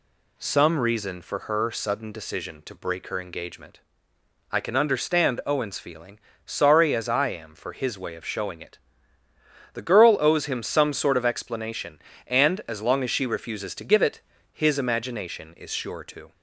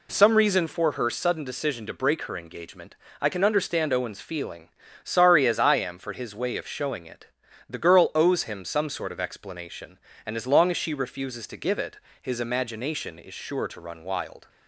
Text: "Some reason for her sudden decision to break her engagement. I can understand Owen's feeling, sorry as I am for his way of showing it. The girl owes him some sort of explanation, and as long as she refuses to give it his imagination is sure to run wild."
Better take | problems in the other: second | pauses between "it" and "his"; slight; at 14.1 s; 0.32 s long; slight in the second // stops before "run wild"; at 16.3 s

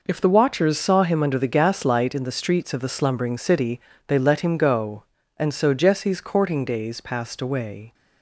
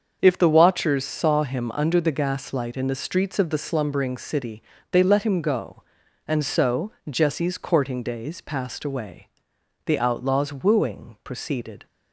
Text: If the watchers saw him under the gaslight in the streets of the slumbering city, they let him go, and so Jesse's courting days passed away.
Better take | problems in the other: first | starts louder than the rest; until 1.2 s; 6.5 dB // pauses between "so" and "Jesse's"; slight; at 6.9 s; 0.18 s long // goes on to say "The outlaw's wooing proceeded"; strong; from 9.8 s on; 2.0 s long

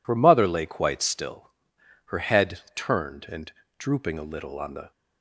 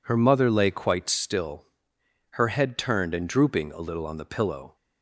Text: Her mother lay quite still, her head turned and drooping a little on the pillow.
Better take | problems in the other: second | pauses between "head" and "turned"; slight; at 2.5 s; 0.16 s long // pauses between "and" and "drooping"; slight; at 3.5 s; 0.26 s long // stops before "pillow"; at 4.9 s

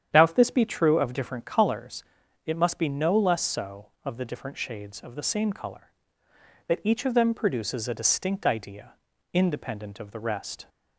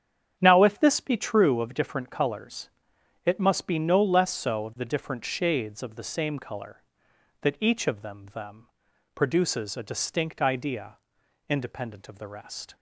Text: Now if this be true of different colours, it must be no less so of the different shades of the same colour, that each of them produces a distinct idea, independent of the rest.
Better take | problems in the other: first | starts louder than the rest; strong; until 1.4 s; 8.5 dB; strong in the first // says "them" twice; at 8.3 s

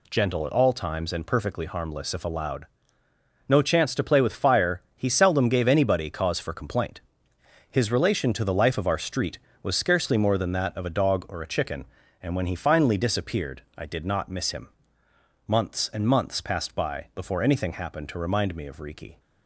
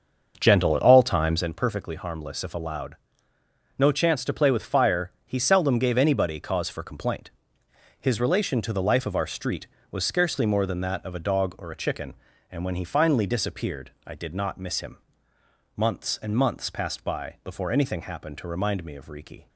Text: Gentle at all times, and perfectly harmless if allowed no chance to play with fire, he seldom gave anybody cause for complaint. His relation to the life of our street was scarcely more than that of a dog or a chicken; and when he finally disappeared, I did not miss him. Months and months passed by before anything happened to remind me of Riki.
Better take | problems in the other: first | starts louder than the rest; until 1.5 s; 6.5 dB // pauses between "allowed" and "no"; noticeable; at 2.9 s; 0.82 s long; noticeable in the first

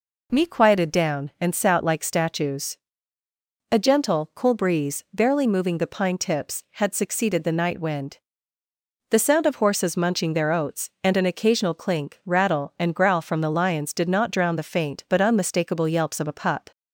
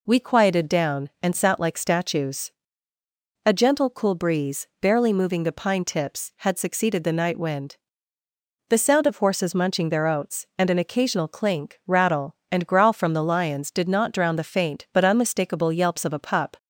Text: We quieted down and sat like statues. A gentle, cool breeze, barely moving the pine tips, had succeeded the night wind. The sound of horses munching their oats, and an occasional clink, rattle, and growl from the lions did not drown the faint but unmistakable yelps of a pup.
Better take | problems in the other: second | says "Me" for "We"; at 0.3 s

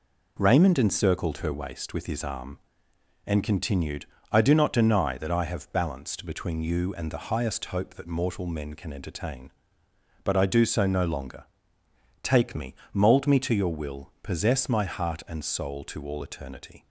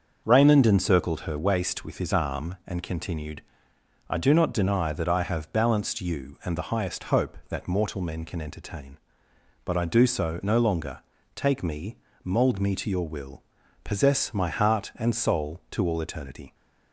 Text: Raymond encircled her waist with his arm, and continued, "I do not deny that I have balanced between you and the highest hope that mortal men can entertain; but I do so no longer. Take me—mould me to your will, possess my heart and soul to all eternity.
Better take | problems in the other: first | starts louder than the rest; until 1.2 s; 6.5 dB // skips "between"; at 6.0 s

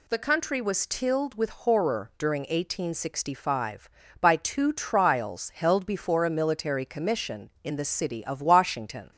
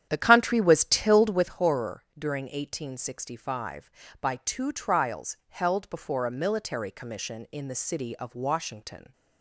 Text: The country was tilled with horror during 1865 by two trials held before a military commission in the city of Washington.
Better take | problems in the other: first | starts louder than the rest; strong; until 1.5 s; 10 dB

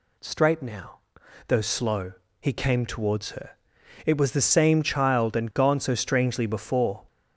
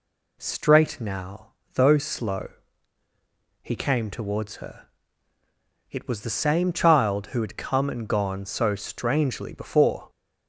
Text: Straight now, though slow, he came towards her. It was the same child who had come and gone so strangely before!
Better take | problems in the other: second | skips "who had come"; at 5.3 s

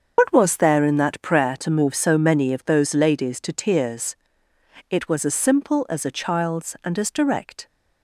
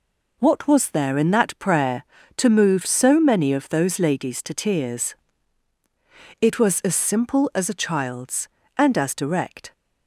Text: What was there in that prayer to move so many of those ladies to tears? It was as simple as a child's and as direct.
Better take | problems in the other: second | loses the start of "What"; at 0.1 s; 55 ms // starts louder than the rest; until 1.1 s; 6.5 dB

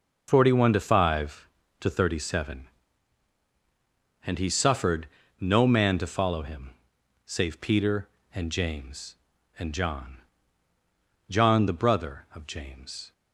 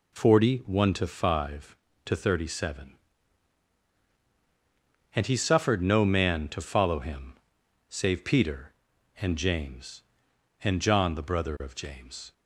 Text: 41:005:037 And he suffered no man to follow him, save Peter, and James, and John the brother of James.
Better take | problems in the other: second | pauses between "suffered" and "no"; slight; at 5.0 s; 0.34 s long // says "John" twice; at 11.2 s

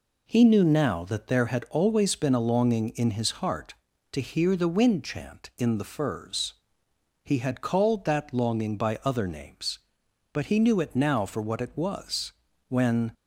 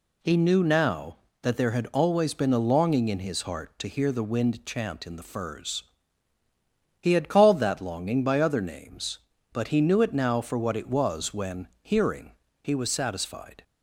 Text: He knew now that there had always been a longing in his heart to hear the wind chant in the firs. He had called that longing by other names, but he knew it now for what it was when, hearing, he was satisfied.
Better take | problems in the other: second | pauses between "was" and "when"; slight; at 12.3 s; 0.34 s long // stops before "hearing he was satisfied"; at 13.1 s

